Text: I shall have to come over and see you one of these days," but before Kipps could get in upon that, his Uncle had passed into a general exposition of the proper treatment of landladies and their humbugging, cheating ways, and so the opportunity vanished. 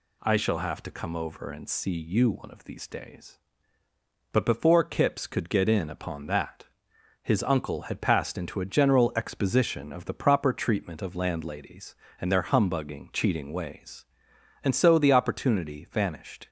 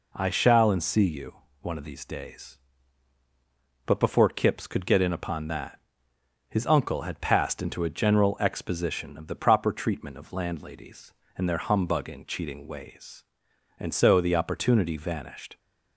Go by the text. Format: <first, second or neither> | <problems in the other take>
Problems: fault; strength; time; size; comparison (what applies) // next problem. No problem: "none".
first | skips "have to come over"; at 0.6 s // pauses between "you" and "one"; slight; at 1.3 s; 0.26 s long